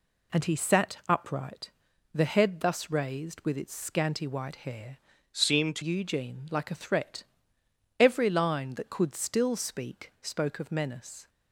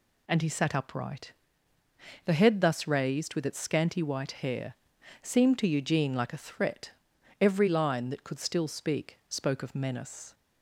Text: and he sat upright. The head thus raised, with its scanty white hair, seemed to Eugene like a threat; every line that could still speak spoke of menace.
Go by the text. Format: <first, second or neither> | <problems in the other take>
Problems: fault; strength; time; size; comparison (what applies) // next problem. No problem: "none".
second | changes voice from "seemed" to "to"; from 5.3 to 5.8 s; 0.5 s long